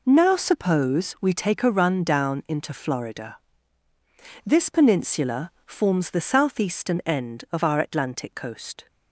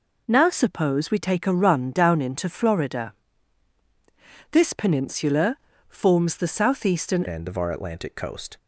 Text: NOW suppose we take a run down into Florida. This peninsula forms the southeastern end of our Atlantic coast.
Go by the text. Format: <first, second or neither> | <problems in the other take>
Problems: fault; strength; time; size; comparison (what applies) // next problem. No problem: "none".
first | pauses between "peninsula" and "forms"; slight; at 5.5 s; 0.32 s long; slight in the first // changes voice at "end"; from 7.2 s on; 1.3 s long